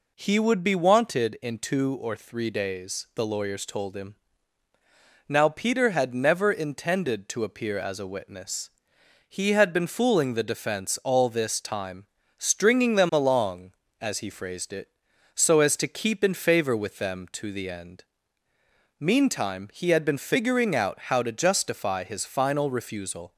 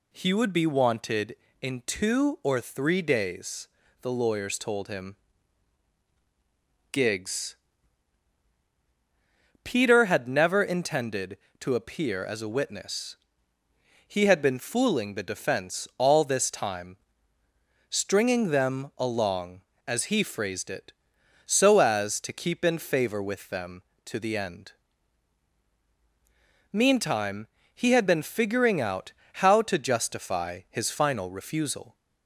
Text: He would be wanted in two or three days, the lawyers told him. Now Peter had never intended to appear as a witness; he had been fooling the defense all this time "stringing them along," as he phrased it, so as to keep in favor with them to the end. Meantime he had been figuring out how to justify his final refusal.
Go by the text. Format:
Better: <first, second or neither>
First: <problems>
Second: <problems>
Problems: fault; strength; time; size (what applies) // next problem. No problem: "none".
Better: first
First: pauses between "time" and "stringing"; slight; at 12.0 s; 0.32 s long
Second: says "Gigs" for "Now"; at 6.9 s // pauses between "time" and "stringing"; noticeable; at 16.9 s; 0.92 s long // pauses between "Meantime" and "he"; slight; at 27.4 s; 0.28 s long // pauses between "out" and "how"; slight; at 29.1 s; 0.22 s long